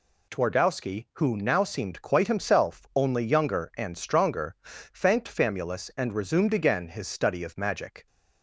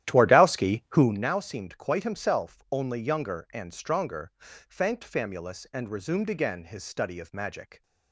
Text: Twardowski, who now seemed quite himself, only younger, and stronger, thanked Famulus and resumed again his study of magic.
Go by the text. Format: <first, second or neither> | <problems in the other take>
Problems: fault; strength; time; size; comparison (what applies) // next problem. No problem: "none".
first | starts louder than the rest; strong; until 1.3 s; 12.5 dB